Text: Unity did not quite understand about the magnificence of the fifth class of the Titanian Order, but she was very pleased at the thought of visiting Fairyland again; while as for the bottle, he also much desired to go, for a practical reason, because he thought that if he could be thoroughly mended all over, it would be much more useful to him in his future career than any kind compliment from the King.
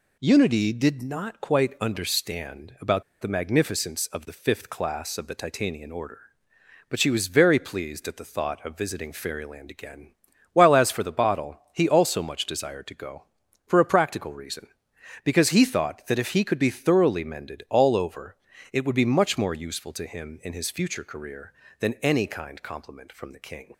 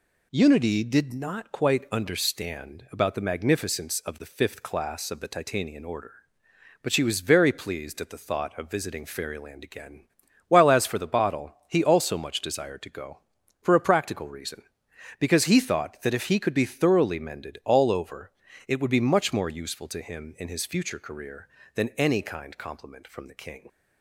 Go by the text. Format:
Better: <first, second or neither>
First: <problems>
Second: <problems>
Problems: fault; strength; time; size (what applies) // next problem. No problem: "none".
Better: second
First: pauses between "about" and "the"; slight; at 3.0 s; 0.18 s long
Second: none